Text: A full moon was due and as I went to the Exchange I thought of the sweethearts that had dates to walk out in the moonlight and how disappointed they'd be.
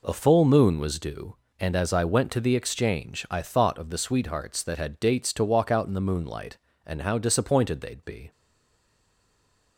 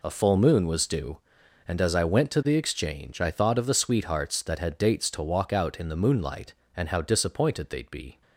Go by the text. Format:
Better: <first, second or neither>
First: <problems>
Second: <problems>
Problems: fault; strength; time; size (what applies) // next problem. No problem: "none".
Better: second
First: stays silent after the last word; noticeable; from 8.3 s on; 1.4 s long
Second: none